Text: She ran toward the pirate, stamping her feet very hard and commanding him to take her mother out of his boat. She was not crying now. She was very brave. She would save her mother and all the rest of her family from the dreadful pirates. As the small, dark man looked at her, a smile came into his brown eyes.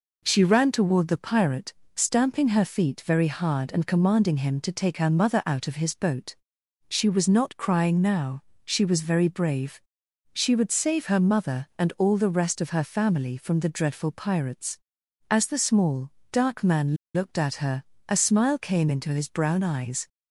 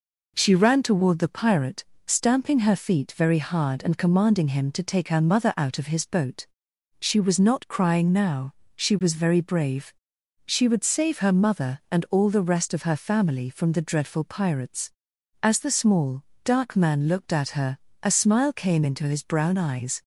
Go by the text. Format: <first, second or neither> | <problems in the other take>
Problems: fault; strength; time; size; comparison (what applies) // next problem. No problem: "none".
second | pauses between "man" and "looked"; slight; at 16.9 s; 0.18 s long